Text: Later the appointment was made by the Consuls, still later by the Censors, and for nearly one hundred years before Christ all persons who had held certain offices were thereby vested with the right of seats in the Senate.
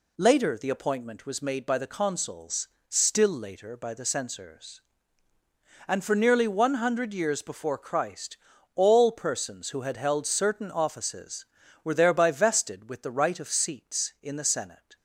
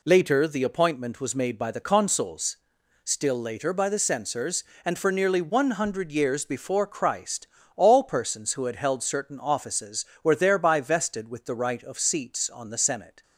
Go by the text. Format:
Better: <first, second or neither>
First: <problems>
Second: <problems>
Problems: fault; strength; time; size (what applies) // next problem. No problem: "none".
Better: first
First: pauses between "Christ" and "all"; at 8.3 s; 0.38 s long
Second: pauses between "Christ" and "all"; slight; at 7.4 s; 0.30 s long // says "on" for "in"; at 12.4 s